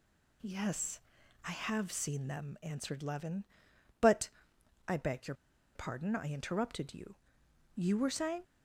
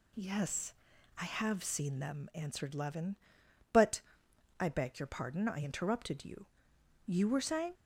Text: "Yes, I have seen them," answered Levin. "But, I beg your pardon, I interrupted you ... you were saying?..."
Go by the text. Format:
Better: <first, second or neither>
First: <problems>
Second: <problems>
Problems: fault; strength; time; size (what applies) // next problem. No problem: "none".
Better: second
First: pauses between "your" and "pardon"; at 5.3 s; 0.41 s long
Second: none